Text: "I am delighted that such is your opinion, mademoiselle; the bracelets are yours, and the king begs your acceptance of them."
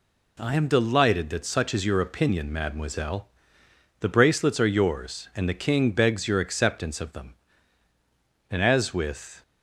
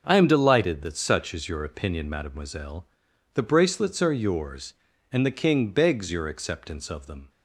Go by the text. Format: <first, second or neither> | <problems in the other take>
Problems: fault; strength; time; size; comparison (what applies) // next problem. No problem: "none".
second | goes on to say "And as with"; noticeable; from 8.4 s on; 0.94 s long